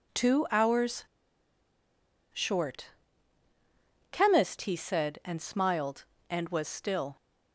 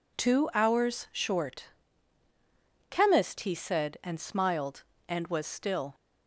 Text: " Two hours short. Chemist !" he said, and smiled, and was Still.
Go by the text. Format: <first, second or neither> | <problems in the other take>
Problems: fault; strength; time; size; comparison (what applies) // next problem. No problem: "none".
second | pauses between "hours" and "short"; strong; at 1.0 s; 1.2 s long